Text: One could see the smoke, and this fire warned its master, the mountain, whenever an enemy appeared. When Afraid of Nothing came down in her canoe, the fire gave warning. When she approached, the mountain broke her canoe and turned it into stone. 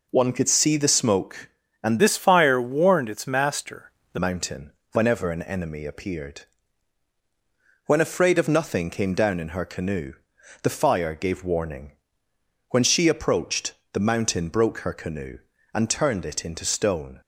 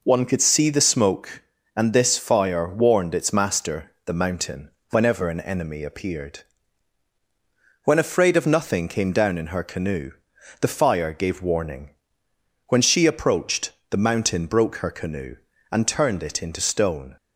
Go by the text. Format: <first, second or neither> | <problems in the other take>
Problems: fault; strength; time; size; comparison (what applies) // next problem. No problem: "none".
second | changes voice from "this" to "the"; from 2.0 to 4.1 s; 2.1 s long